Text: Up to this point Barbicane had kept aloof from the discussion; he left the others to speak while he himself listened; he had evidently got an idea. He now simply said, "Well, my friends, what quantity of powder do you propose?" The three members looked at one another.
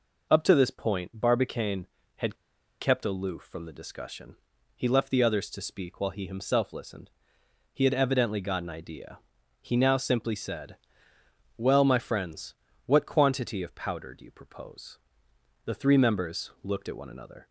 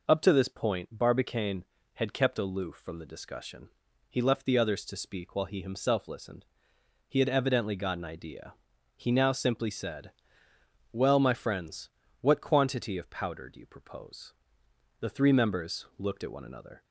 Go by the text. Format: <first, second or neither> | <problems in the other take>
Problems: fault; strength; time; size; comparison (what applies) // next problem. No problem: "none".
second | pauses between "had" and "kept"; at 2.3 s; 0.44 s long